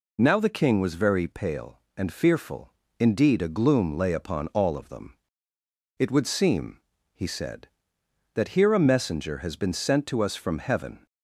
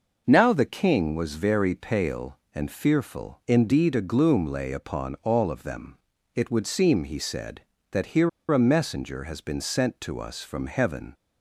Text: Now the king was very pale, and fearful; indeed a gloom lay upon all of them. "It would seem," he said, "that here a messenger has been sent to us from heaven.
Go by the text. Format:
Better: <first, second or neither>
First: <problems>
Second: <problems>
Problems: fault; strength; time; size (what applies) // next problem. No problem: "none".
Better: first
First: none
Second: pauses between "here" and "a"; slight; at 8.2 s; 0.22 s long